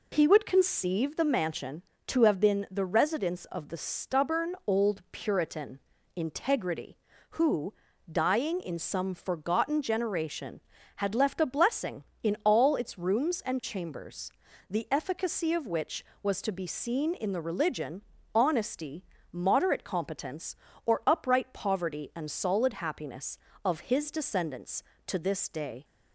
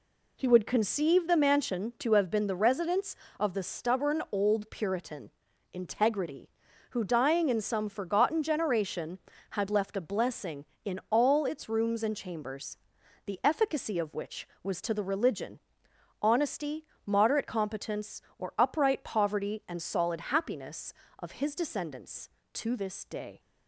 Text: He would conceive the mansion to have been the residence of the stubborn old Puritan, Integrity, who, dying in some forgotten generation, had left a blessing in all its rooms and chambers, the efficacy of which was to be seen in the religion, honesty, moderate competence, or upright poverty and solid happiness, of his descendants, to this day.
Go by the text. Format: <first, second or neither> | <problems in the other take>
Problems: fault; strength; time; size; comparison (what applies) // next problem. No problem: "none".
first | skips "be seen in"; at 14.9 s